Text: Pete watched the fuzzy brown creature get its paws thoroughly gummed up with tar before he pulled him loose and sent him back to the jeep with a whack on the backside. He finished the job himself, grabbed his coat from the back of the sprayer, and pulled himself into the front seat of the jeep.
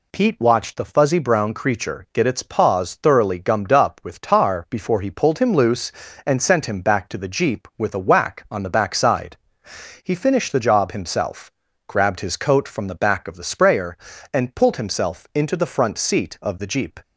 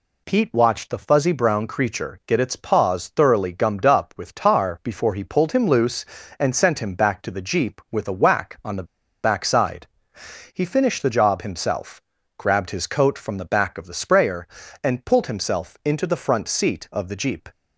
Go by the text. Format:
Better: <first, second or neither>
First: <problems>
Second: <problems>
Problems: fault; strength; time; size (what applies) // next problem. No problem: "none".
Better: first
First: none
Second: pauses between "the" and "backside"; at 8.8 s; 0.39 s long